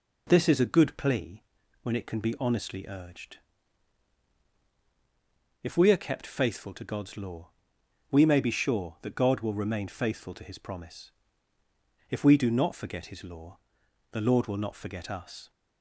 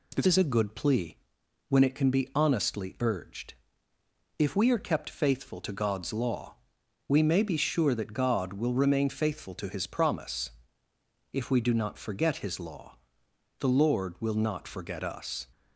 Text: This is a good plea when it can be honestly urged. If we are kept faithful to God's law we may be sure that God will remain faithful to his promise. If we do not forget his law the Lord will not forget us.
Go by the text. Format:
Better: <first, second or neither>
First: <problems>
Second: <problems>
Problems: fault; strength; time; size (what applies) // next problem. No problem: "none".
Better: first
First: pauses between "plea" and "when"; at 1.4 s; 0.42 s long // pauses between "law" and "we"; noticeable; at 7.4 s; 0.62 s long // pauses between "law" and "the"; noticeable; at 13.5 s; 0.52 s long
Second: changes voice at "is"; from 0.2 s on; 15.2 s long // pauses between "plea" and "when"; noticeable; at 1.1 s; 0.54 s long // pauses between "law" and "we"; noticeable; at 6.5 s; 0.52 s long // pauses between "law" and "the"; noticeable; at 12.9 s; 0.64 s long